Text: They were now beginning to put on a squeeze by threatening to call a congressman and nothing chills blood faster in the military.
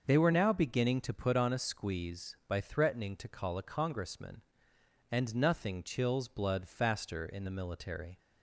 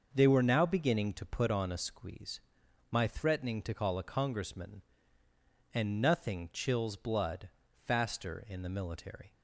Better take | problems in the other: first | starts louder than the rest; noticeable; until 1.1 s; 6 dB; also in the first // says "my" for "by"; at 2.9 s // pauses between "blood" and "faster"; slight; at 7.4 s; 0.36 s long

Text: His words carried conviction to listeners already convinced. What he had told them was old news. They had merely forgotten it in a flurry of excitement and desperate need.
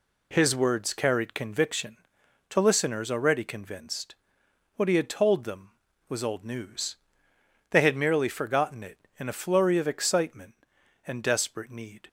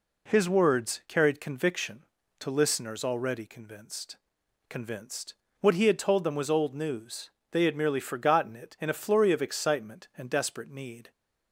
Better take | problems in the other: first | says "convinced" twice; at 4.6 s

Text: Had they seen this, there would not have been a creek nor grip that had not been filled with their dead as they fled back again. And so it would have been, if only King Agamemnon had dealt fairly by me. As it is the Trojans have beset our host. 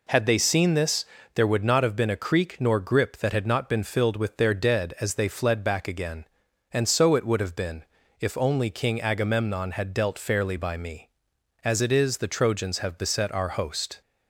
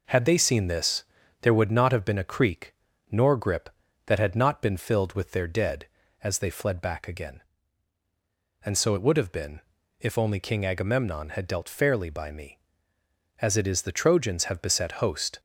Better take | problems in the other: first | pauses between "creek" and "nor"; slight; at 2.7 s; 0.36 s long // skips "our"; at 14.9 s

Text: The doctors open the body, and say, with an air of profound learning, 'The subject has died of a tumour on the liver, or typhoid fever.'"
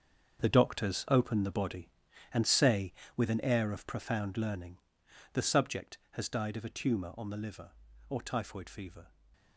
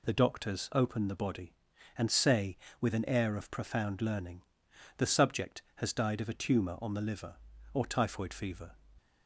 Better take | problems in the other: second | gets quieter; strong; throughout; 11 dB

